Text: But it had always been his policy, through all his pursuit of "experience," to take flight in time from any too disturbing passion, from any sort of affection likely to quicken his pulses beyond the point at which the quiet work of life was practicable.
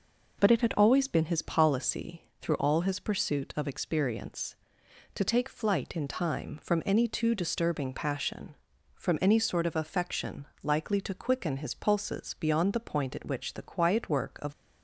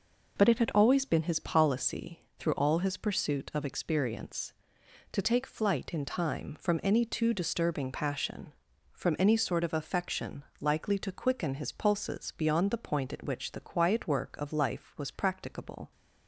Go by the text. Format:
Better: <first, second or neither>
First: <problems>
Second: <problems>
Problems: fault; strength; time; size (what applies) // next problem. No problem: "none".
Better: second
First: pauses between "affection" and "likely"; slight; at 10.4 s; 0.16 s long // stops before "life was practicable"; at 14.5 s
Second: pauses between "affection" and "likely"; slight; at 10.4 s; 0.16 s long